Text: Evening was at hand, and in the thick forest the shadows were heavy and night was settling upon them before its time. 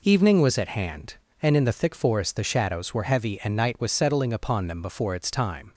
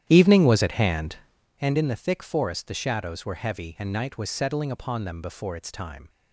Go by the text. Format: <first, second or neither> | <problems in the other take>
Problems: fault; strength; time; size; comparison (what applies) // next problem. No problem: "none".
first | starts louder than the rest; strong; until 1.6 s; 11 dB